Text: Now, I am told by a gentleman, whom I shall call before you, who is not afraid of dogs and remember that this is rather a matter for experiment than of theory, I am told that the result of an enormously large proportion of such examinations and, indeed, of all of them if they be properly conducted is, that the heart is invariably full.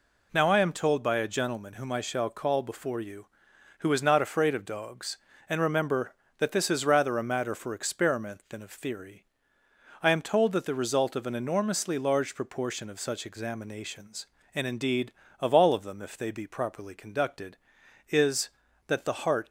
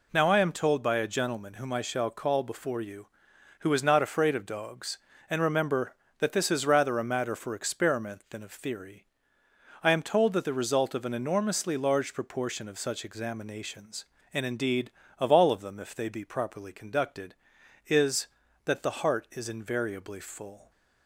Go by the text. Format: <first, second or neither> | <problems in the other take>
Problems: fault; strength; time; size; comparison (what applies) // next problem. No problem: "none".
second | stops before "is invariably full"; at 19.4 s